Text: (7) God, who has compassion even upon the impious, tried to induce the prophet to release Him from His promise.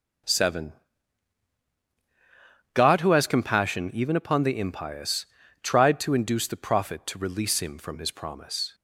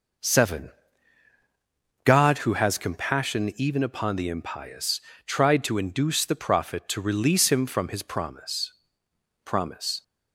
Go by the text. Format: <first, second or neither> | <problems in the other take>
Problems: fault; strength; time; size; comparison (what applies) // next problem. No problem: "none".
first | says "promise" twice; at 9.4 s